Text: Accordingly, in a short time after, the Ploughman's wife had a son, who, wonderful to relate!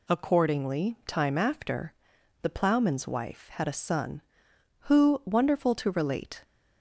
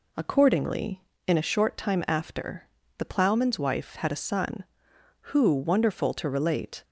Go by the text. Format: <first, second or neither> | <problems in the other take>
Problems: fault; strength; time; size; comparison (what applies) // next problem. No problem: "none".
second | skips "in a short"; at 1.0 s